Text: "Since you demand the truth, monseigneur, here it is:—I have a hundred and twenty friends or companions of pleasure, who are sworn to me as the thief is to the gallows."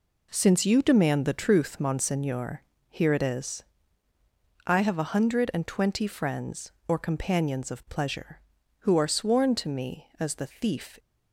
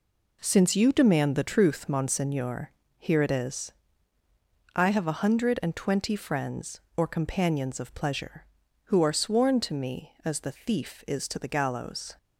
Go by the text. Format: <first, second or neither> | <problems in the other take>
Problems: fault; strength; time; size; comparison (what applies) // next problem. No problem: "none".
second | stops before "is to the gallows"; at 10.9 s